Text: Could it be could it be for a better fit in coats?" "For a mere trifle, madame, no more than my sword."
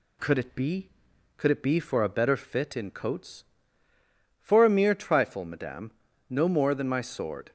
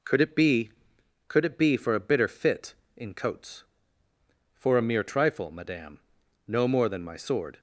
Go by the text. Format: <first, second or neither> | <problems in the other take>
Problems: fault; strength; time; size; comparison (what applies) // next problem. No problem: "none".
first | says "bitter" for "better"; at 1.9 s